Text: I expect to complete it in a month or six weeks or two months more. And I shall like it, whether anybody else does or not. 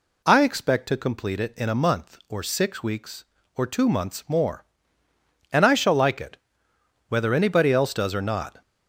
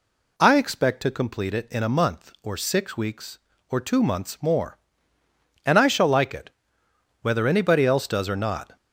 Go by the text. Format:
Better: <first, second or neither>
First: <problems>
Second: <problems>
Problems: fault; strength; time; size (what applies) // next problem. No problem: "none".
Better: neither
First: none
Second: none